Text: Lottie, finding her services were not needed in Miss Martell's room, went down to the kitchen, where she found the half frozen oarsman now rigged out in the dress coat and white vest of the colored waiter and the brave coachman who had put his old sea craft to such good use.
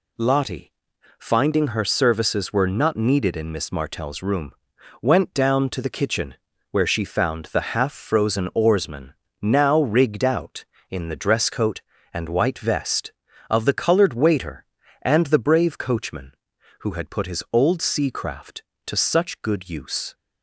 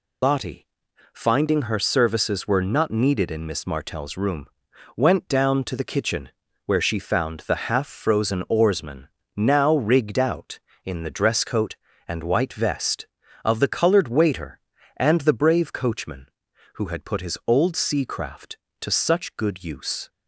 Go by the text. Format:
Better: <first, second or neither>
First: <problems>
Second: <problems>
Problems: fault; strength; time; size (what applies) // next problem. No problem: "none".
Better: first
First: pauses between "oarsman" and "now"; slight; at 9.1 s; 0.26 s long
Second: loses the start of "Lottie"; at 0.2 s; 100 ms // pauses between "oarsman" and "now"; slight; at 9.0 s; 0.26 s long